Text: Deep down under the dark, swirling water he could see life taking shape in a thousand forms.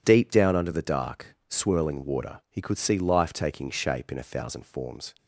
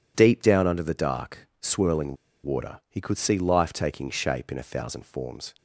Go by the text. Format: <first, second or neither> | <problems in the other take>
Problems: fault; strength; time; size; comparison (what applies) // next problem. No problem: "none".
first | pauses between "swirling" and "water"; slight; at 2.1 s; 0.27 s long